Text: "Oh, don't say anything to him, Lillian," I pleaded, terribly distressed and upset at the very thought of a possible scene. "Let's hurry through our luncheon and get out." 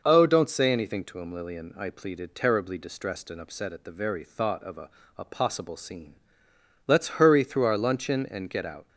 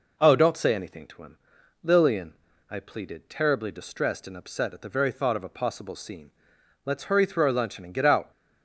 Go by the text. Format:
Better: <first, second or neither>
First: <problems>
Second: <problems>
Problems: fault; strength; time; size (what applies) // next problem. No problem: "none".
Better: second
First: says "a" twice; at 5.1 s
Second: none